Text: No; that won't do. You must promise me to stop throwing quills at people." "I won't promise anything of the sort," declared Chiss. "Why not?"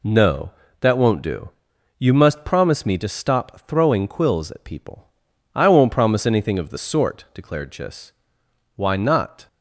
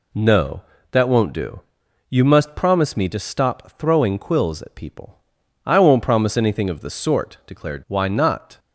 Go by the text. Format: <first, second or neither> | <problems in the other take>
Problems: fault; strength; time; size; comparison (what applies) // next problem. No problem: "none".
first | skips "Chiss"; at 7.8 s